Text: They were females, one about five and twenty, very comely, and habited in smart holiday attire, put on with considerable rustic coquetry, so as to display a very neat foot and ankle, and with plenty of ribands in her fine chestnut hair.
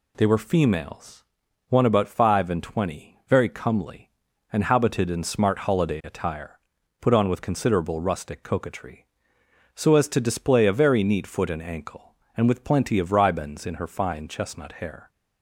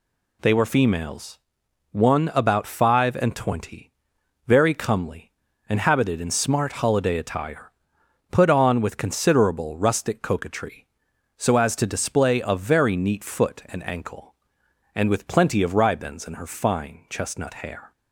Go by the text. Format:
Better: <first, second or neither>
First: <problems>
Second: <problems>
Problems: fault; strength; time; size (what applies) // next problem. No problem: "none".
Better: neither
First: none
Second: none